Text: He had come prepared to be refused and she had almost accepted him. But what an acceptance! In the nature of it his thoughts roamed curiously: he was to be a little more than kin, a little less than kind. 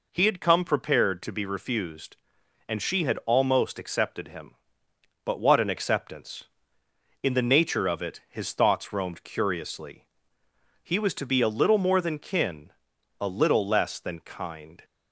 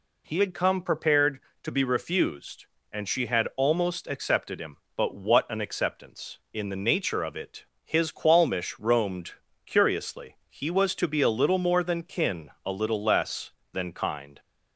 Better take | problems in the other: first | pauses between "it" and "his"; slight; at 7.6 s; 0.20 s long // says "qualmish" for "thoughts"; at 8.0 s // pauses between "roamed" and "curiously"; slight; at 9.3 s; 0.34 s long

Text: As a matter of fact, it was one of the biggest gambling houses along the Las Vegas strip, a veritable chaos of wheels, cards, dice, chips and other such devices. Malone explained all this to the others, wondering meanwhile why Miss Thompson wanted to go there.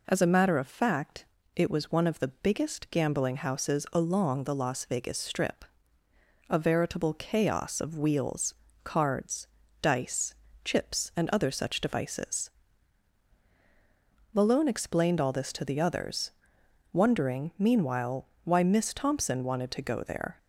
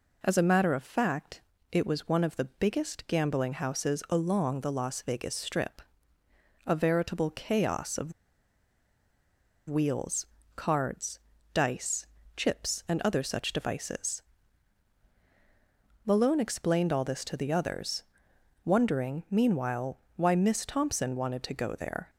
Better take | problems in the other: first | pauses between "of" and "wheels"; strong; at 8.1 s; 1.5 s long // pauses between "meanwhile" and "why"; slight; at 19.9 s; 0.18 s long; slight in the first

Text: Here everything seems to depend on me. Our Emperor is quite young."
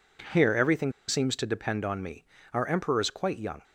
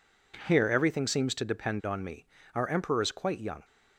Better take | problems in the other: second | pauses between "everything" and "seems"; slight; at 0.9 s; 0.16 s long

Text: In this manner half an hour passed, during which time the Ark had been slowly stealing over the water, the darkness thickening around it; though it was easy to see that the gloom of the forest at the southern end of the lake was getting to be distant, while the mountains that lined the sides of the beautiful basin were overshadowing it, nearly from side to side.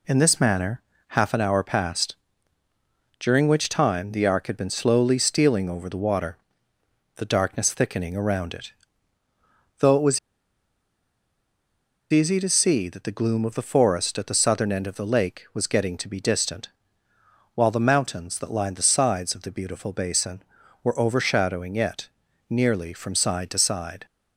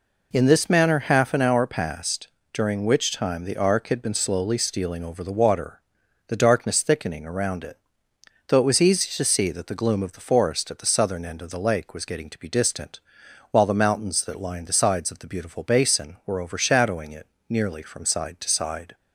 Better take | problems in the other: second | pauses between "manner" and "half"; slight; at 0.8 s; 0.26 s long // pauses between "was" and "easy"; strong; at 10.1 s; 1.9 s long

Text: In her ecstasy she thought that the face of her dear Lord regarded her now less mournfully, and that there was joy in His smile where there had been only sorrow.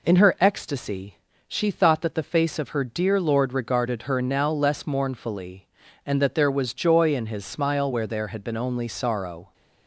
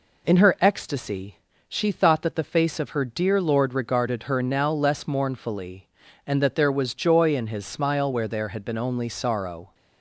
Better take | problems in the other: neither | pauses between "ecstasy" and "she"; slight; the same in both

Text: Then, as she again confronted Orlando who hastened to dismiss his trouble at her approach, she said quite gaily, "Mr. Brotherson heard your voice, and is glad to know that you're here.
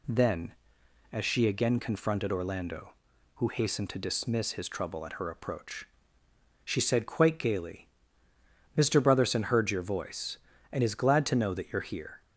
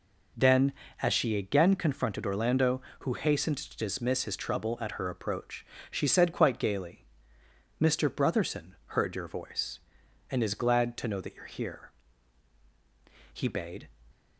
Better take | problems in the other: first | goes on to say "He bade"; from 13.3 s on; 0.58 s long

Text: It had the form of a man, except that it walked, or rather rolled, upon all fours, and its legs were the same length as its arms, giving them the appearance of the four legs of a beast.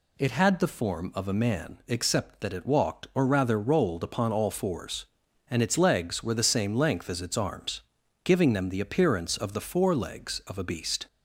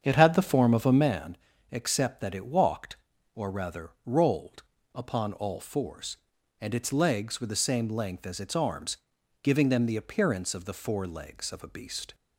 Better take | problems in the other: first | starts louder than the rest; strong; until 1.2 s; 8 dB

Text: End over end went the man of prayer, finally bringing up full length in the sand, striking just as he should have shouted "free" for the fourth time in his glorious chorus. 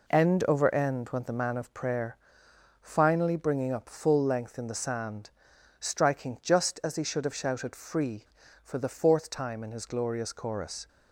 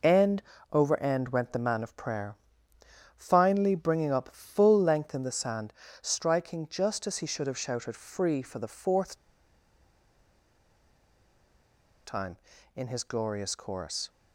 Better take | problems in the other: first | pauses between "End" and "over"; slight; at 0.4 s; 0.32 s long // pauses between "fourth" and "time"; strong; at 9.1 s; 2.9 s long

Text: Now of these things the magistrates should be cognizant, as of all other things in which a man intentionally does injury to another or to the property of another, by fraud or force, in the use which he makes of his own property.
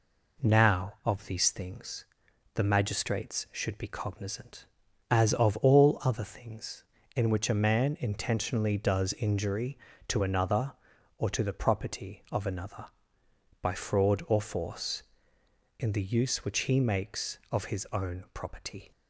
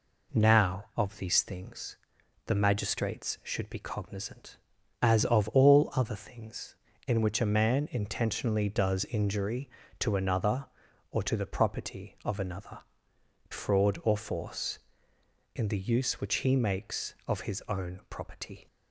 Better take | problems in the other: first | pauses between "things" and "the"; noticeable; at 1.9 s; 0.50 s long; noticeable in the first // skips "by"; at 13.1 s

